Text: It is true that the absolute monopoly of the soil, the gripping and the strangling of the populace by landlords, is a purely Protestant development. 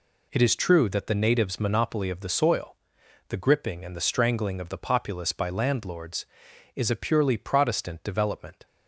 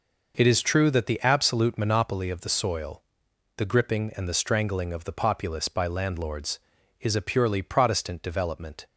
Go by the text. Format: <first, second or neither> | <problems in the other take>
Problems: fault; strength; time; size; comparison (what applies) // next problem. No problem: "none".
second | says "natives" for "absolute"; at 1.1 s